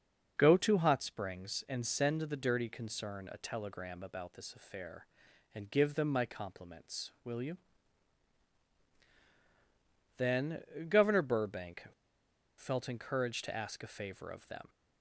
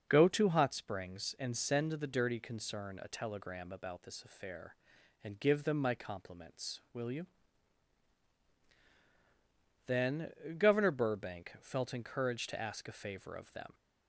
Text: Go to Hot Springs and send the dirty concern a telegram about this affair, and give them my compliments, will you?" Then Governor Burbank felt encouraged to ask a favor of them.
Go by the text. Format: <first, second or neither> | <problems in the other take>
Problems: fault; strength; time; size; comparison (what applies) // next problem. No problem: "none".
second | starts louder than the rest; noticeable; until 1.3 s; 6 dB; noticeable in the second // pauses between "Then" and "Governor"; slight; at 10.6 s; 0.26 s long; slight in the second // pauses between "Burbank" and "felt"; noticeable; at 11.8 s; 0.73 s long